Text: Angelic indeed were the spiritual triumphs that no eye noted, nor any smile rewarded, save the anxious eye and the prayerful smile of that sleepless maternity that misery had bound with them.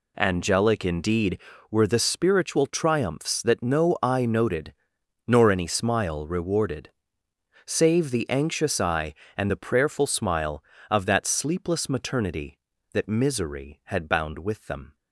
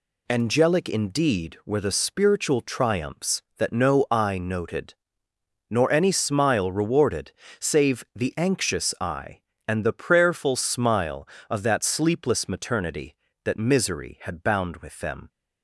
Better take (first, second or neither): neither